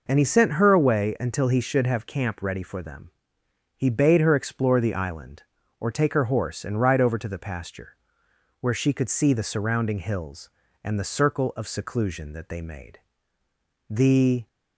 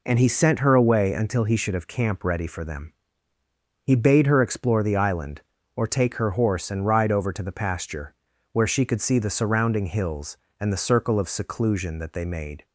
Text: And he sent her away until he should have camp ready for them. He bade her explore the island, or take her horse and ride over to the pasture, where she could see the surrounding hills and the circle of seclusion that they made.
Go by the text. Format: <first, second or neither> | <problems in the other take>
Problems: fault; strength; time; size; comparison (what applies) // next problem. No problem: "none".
second | goes on to say "The"; from 13.8 s on; 0.58 s long